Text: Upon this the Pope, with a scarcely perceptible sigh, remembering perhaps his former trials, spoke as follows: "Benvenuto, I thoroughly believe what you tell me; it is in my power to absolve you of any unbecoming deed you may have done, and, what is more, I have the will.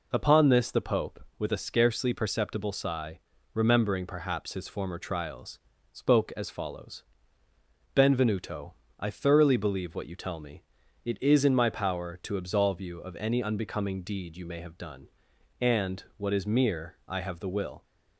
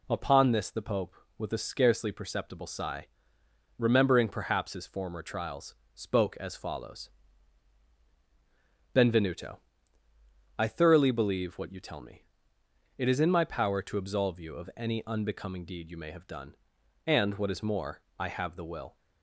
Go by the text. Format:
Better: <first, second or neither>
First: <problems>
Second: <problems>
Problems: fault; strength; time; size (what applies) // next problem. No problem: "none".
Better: second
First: says "mere" for "more"; at 16.4 s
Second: none